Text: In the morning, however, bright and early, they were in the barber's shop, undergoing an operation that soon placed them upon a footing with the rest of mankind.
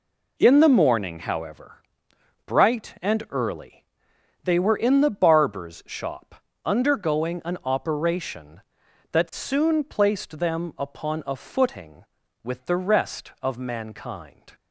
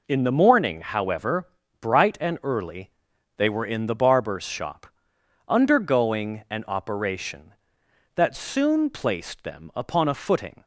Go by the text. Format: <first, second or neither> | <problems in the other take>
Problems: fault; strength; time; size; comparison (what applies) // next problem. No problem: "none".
first | stops before "with the rest of mankind"; at 10.6 s